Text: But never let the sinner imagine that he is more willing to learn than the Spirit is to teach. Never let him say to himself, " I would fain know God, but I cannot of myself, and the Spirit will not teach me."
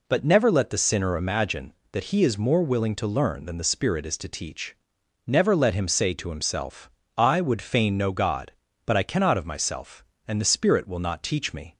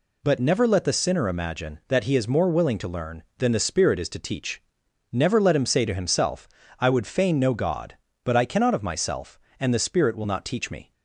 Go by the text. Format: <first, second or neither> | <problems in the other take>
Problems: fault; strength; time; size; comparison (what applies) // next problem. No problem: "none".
neither | none